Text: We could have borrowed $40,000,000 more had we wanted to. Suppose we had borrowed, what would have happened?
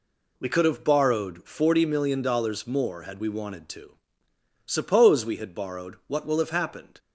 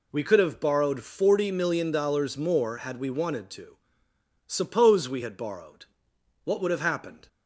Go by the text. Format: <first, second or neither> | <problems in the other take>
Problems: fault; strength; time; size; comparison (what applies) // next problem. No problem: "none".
second | says "will" for "would"; at 6.2 s